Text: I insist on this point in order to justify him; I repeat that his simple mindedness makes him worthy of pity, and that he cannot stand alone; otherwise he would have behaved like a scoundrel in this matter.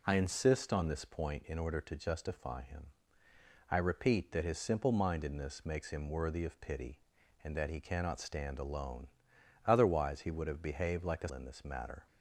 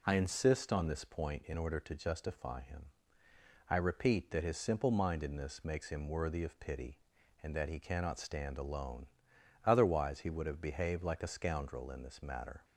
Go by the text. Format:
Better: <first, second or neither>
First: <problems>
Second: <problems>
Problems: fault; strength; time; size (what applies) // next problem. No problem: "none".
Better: second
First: skips "scoundrel"; at 11.2 s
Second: none